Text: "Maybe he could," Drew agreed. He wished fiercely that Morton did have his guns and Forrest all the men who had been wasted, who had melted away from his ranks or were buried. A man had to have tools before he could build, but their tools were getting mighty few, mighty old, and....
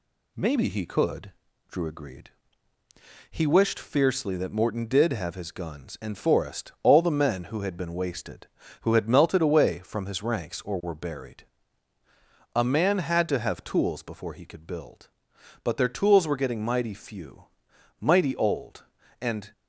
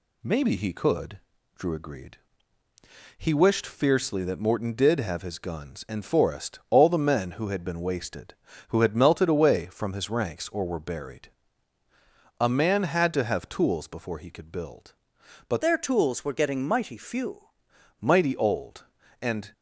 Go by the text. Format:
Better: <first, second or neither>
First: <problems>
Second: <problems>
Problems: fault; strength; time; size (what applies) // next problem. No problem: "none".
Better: first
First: none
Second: changes voice from "their" to "few"; from 15.6 to 17.4 s; 1.8 s long